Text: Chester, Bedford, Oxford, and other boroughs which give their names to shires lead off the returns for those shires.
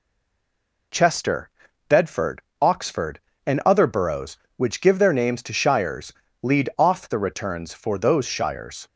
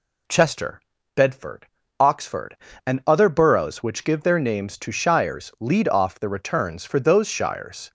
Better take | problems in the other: second | stays silent before the first word; slight; until 0.9 s; 0.9 s long // pauses between "shires" and "lead"; slight; at 6.1 s; 0.30 s long

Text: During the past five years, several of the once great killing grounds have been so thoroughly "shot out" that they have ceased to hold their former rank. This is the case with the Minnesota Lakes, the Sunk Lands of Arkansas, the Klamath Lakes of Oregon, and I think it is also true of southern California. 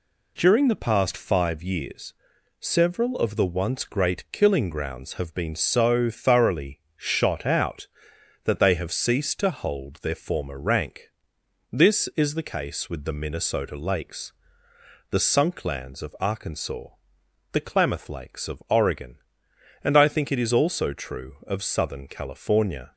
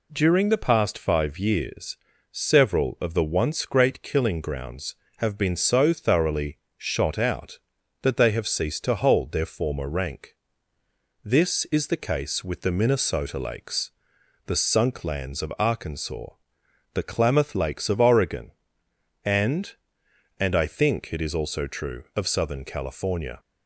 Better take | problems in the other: first | pauses between "thoroughly" and "shot"; slight; at 6.5 s; 0.20 s long; slight in the first // says "and" twice; at 20.3 s

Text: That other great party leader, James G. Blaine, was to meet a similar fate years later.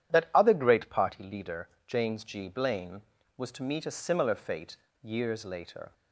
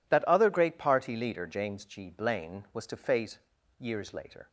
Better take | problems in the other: first | skips "meet a similar"; at 2.9 s // pauses between "fate" and "years"; at 3.3 s; 0.40 s long; slight in the first

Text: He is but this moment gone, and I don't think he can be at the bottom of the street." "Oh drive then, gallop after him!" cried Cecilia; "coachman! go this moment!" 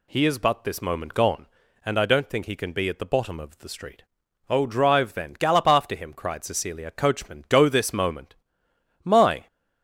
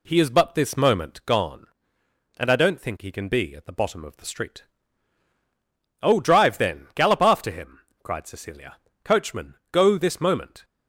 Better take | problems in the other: second | goes on to say "My"; slight; from 9.0 s on; 0.44 s long

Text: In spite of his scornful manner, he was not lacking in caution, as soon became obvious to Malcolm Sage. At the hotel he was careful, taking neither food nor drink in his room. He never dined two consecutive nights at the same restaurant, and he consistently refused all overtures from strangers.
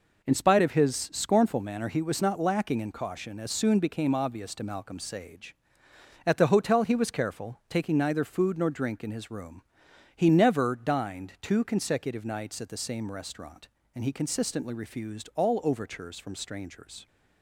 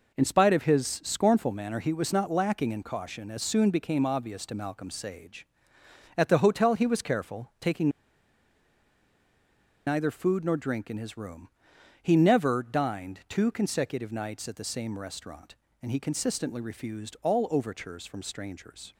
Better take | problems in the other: first | pauses between "taking" and "neither"; strong; at 7.8 s; 1.9 s long

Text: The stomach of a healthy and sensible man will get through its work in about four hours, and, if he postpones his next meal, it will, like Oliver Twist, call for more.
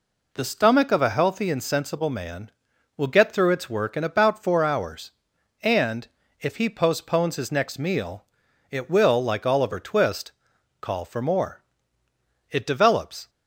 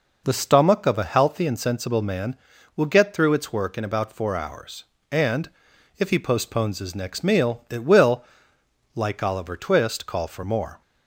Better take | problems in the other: second | goes on to say "It develops"; noticeable; from 12.4 s on; 0.80 s long

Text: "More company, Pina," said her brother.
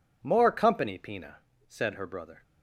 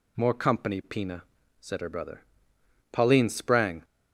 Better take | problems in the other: first | goes on to say "Pauline sprang"; noticeable; from 2.9 s on; 0.94 s long

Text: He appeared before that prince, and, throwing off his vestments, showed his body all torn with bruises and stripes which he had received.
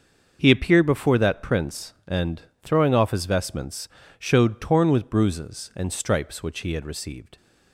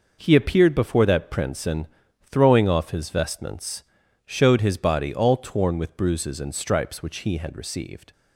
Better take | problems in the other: second | starts louder than the rest; until 1.4 s; 6.5 dB // skips "his body all"; at 4.5 s

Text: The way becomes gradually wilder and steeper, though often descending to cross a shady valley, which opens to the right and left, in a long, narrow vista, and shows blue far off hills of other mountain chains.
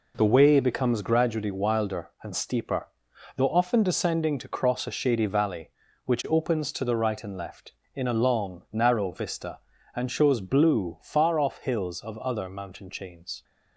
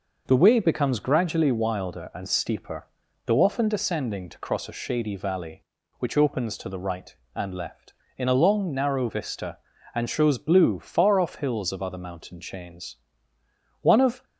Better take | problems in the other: first | goes on to say "One of"; slight; from 13.8 s on; 0.42 s long

